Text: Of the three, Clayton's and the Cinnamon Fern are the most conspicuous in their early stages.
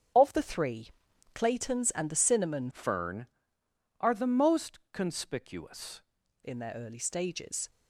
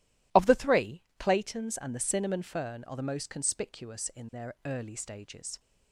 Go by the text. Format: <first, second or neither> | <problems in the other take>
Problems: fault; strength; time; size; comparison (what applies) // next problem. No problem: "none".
second | starts louder than the rest; strong; until 1.6 s; 7.5 dB // changes voice from "Fern" to "conspicuous"; from 2.7 to 6.0 s; 3.3 s long